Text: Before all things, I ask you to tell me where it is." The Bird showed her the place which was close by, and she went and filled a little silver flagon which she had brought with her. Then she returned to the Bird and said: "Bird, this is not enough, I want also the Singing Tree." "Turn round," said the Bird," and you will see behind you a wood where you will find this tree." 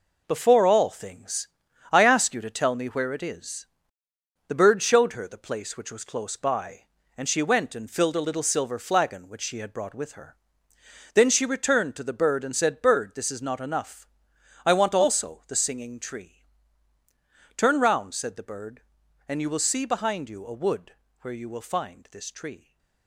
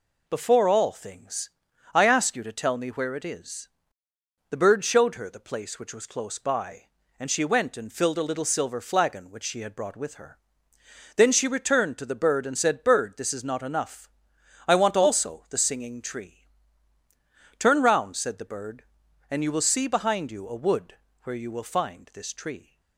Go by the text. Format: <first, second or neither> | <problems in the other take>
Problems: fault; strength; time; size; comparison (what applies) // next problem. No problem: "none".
second | gets quieter; strong; throughout; 8 dB // pauses between "wood" and "where"; slight; at 20.9 s; 0.26 s long; slight in the second